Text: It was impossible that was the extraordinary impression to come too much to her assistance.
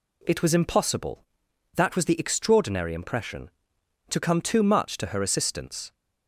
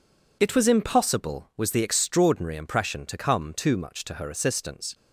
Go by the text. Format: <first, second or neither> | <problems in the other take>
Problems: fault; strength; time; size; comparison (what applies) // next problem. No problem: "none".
first | skips "that"; at 1.5 s